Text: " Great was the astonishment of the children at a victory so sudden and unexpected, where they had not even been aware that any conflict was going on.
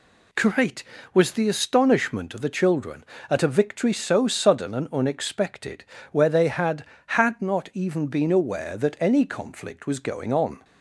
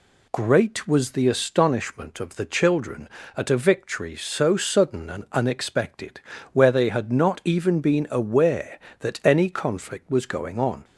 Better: second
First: says "had" twice; at 7.0 s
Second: none

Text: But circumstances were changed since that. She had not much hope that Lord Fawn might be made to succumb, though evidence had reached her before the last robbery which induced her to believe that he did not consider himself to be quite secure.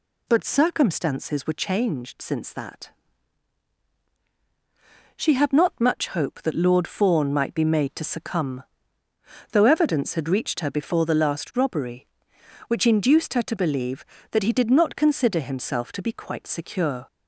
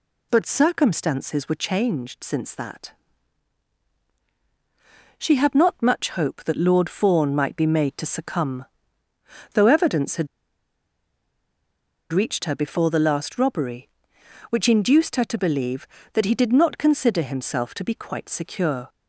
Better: first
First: none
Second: pauses between "had" and "reached"; strong; at 10.2 s; 1.8 s long

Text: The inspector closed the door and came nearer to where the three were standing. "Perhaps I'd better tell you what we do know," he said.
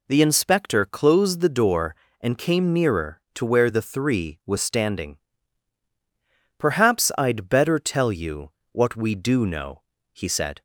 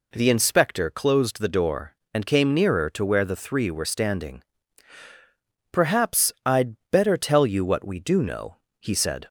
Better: second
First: says "was" for "were"; at 4.4 s // pauses between "you" and "what"; slight; at 8.4 s; 0.22 s long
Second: none

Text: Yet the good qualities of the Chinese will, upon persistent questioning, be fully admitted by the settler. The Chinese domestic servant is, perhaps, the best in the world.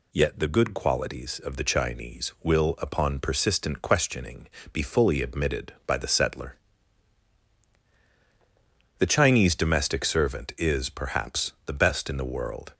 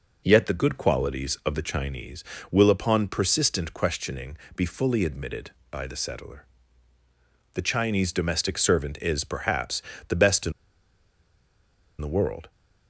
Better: first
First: none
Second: pauses between "in" and "the"; strong; at 10.5 s; 1.4 s long

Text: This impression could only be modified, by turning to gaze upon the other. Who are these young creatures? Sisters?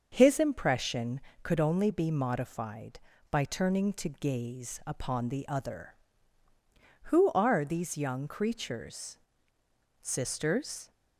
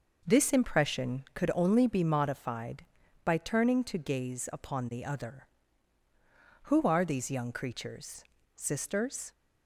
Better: second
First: starts louder than the rest; until 1.1 s; 6.5 dB // says "His" for "This"; at 0.1 s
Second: none

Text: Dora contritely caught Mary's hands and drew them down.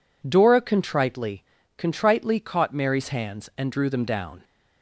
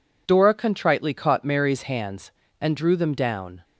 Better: second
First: says "contritely" twice; at 1.7 s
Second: none

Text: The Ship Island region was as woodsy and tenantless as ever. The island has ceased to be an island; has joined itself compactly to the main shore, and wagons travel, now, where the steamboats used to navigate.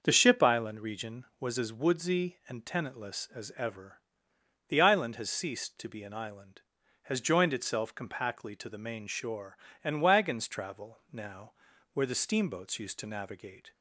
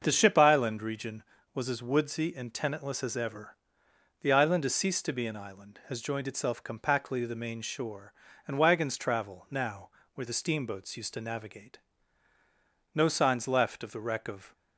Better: first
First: starts louder than the rest; until 1.0 s; 6 dB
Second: starts louder than the rest; until 1.0 s; 6.5 dB // goes on to say "No signs left of the wreck of"; from 12.9 s on; 1.6 s long

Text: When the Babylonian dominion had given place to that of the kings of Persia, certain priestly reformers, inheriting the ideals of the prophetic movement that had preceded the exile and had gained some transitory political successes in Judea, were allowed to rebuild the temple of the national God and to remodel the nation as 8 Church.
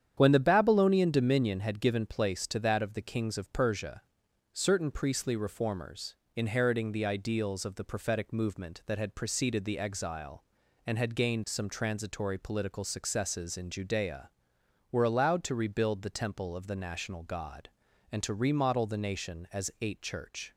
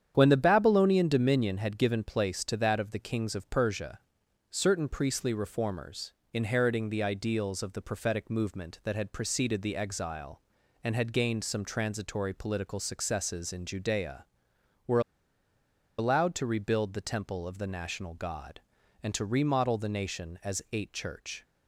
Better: first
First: starts louder than the rest; strong; until 1.1 s; 9 dB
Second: starts louder than the rest; strong; until 1.1 s; 9 dB // pauses between "were" and "allowed"; at 14.9 s; 0.98 s long

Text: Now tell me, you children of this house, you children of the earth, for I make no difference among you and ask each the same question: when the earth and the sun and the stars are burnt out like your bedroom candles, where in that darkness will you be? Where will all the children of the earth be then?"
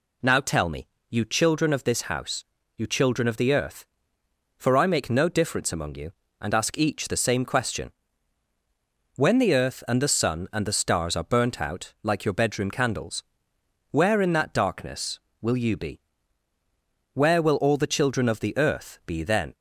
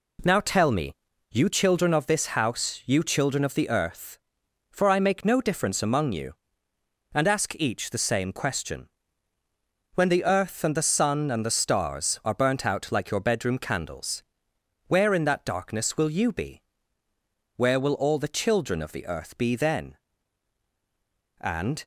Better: first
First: none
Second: goes on to say "And"; slight; from 21.4 s on; 0.44 s long

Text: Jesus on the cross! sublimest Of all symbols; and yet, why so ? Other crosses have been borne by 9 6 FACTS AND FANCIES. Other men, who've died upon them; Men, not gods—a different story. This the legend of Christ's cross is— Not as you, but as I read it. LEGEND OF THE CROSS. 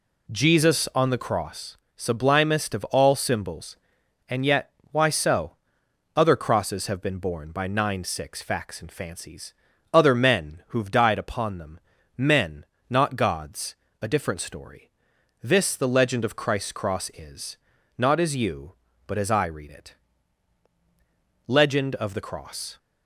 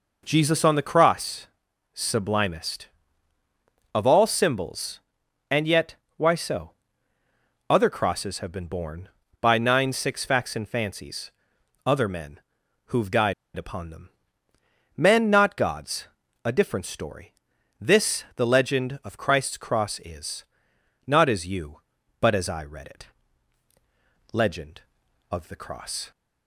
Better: first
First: none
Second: pauses between "died" and "upon"; slight; at 13.3 s; 0.23 s long

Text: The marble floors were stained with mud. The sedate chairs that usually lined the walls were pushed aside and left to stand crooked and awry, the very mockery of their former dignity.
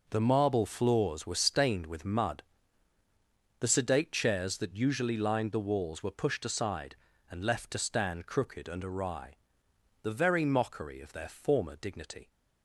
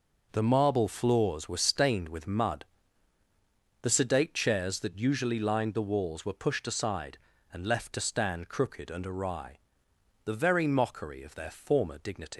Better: first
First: none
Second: leaves "dignity" unfinished; at 12.3 s; 130 ms

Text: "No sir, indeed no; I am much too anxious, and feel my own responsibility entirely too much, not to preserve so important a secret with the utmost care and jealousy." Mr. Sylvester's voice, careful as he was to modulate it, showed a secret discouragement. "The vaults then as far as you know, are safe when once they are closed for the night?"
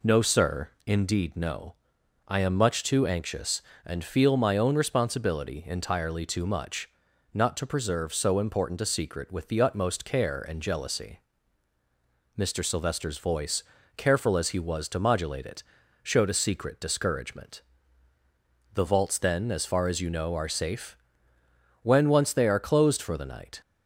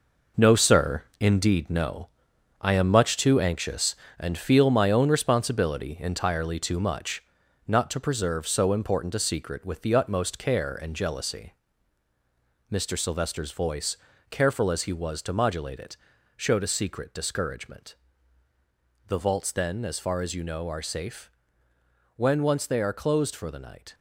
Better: first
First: pauses between "safe" and "when"; noticeable; at 20.9 s; 0.86 s long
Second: gets quieter; strong; throughout; 8.5 dB // pauses between "safe" and "when"; noticeable; at 21.3 s; 0.86 s long

